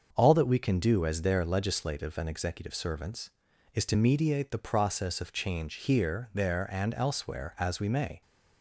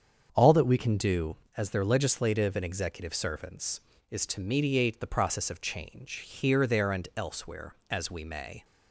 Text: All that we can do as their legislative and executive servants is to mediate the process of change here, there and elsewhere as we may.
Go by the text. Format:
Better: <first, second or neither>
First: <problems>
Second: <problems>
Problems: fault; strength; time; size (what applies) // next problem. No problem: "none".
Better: first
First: starts louder than the rest; until 1.1 s; 6.5 dB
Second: starts louder than the rest; strong; until 1.3 s; 7.5 dB // changes voice at "can"; from 0.7 s on; 7.9 s long